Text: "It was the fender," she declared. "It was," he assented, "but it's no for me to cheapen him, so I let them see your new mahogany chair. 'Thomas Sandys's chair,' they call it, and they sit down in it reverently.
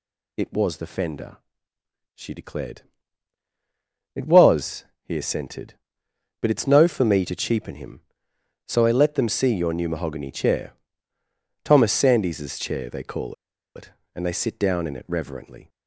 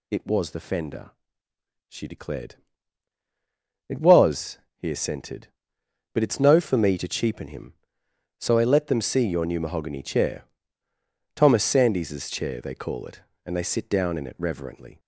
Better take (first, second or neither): second